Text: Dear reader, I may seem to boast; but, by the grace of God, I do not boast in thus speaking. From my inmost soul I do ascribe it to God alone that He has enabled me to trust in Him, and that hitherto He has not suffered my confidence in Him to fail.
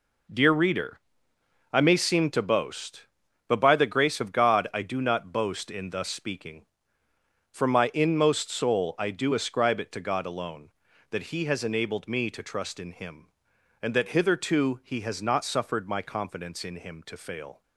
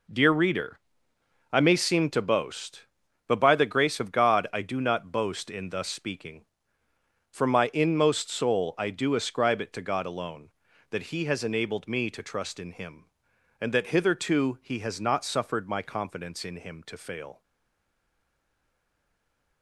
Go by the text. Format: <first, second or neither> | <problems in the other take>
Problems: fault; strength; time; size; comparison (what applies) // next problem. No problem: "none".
first | stays silent after the last word; from 17.4 s on; 2.2 s long